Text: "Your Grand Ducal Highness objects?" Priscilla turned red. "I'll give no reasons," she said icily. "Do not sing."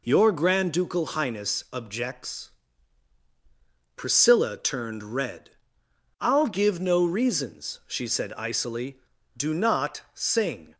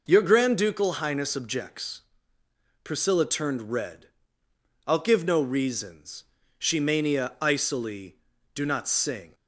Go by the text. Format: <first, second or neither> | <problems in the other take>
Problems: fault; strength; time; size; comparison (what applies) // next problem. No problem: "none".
first | says "mania" for "said"; at 6.7 s